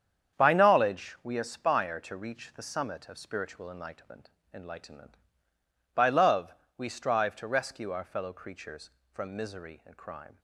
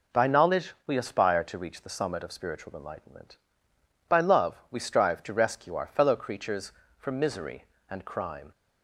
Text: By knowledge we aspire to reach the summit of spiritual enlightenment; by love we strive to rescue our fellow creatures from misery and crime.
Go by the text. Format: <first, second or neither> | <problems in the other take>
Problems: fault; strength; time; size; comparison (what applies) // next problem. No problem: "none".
second | starts louder than the rest; strong; until 1.4 s; 8 dB // says "enlightenment" twice; at 4.5 s // pauses between "love" and "we"; slight; at 6.5 s; 0.20 s long